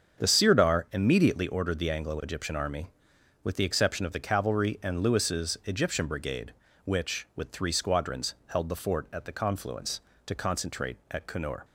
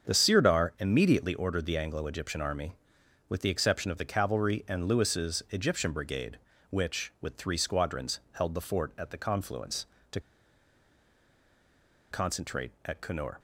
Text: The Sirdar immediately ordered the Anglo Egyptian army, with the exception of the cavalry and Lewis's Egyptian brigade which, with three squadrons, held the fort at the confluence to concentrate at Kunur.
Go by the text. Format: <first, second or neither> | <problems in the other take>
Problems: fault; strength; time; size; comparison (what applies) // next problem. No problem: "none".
first | starts louder than the rest; until 1.1 s; 7 dB; strong in the first // pauses between "to" and "concentrate"; strong; at 10.1 s; 1.9 s long